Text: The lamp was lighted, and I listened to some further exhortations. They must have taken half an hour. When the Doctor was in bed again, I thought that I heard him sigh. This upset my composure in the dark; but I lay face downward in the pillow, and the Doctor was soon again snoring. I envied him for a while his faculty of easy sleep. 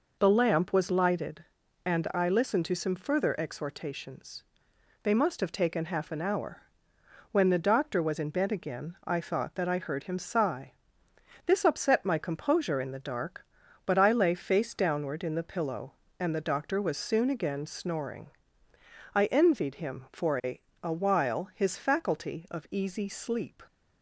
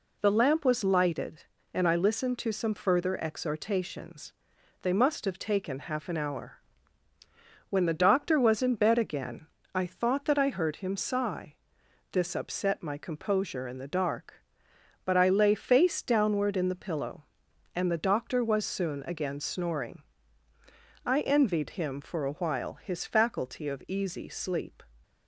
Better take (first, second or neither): second